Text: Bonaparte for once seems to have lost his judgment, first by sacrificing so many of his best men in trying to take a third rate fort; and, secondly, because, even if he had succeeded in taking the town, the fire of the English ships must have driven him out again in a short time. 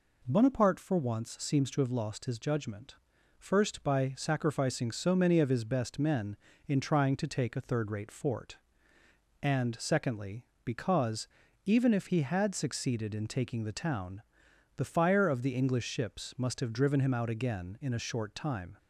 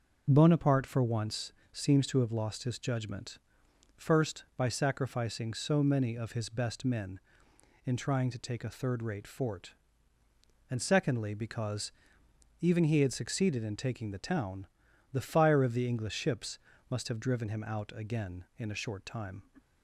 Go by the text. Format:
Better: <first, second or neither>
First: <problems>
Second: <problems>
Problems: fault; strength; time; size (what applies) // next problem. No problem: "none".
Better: first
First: none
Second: pauses between "once" and "seems"; slight; at 1.5 s; 0.20 s long // skips "if"; at 12.8 s // pauses between "ships" and "must"; slight; at 16.5 s; 0.32 s long